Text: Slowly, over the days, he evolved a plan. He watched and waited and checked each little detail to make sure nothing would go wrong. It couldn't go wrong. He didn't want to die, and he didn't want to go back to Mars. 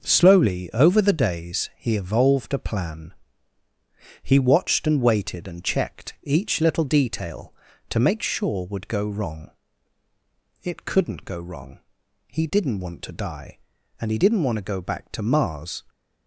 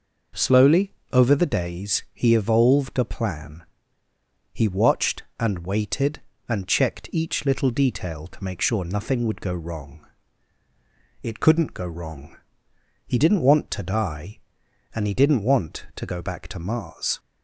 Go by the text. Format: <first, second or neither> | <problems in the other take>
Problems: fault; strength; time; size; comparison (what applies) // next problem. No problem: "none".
second | skips "nothing"; at 8.6 s